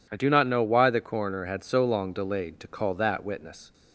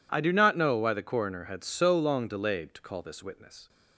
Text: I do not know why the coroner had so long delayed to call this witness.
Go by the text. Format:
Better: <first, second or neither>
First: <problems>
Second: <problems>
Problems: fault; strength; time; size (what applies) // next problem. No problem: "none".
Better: second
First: says "that" for "this"; at 2.9 s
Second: none